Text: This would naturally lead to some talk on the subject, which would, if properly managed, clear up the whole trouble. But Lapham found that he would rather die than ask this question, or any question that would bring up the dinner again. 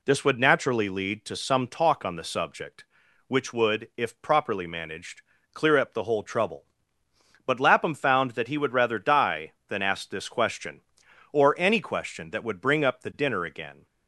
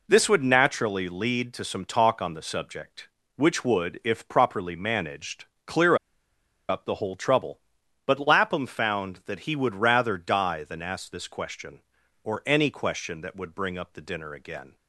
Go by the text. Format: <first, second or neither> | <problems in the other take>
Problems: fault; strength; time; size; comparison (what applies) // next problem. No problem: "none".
first | pauses between "clear" and "up"; noticeable; at 5.9 s; 0.73 s long